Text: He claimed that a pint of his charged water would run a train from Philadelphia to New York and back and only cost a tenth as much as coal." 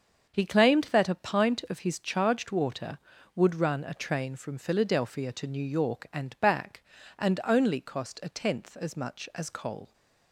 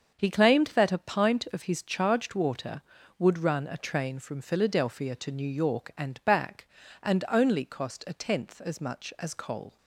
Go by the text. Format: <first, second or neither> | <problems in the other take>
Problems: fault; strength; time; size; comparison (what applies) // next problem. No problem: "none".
neither | starts louder than the rest; the same in both